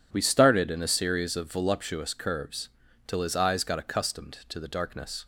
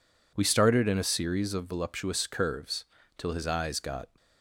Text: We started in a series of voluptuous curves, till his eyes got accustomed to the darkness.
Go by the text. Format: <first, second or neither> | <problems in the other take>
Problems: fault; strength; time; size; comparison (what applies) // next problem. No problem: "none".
first | stops before "accustomed to the darkness"; at 4.1 s